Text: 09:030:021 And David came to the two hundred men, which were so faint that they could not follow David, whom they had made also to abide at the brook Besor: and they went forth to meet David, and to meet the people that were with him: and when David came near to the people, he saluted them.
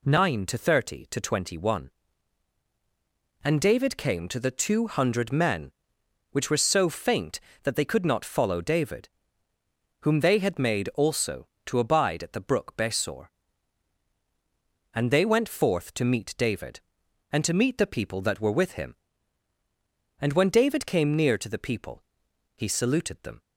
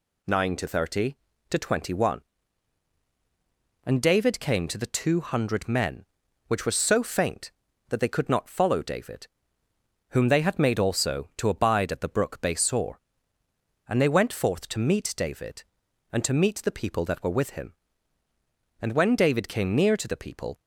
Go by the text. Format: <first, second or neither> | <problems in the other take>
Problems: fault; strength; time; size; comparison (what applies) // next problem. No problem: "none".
first | stops before "he saluted them"; at 20.6 s